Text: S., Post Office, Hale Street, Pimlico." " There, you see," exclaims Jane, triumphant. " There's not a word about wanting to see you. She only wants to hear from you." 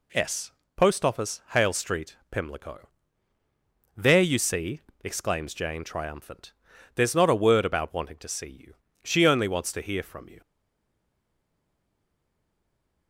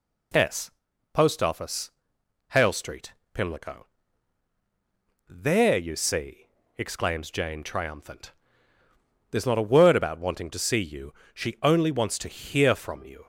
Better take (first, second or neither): second